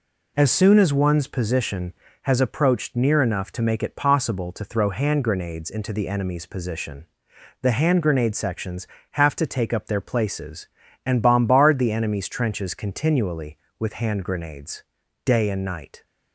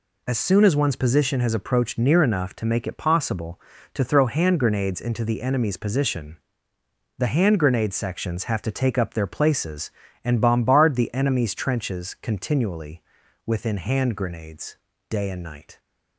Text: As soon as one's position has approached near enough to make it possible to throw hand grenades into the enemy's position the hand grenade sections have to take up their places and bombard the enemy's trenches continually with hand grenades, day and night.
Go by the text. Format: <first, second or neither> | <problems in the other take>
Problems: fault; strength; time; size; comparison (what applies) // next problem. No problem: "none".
first | pauses between "position" and "the"; noticeable; at 6.3 s; 0.82 s long; noticeable in the first // says "within" for "with"; at 13.4 s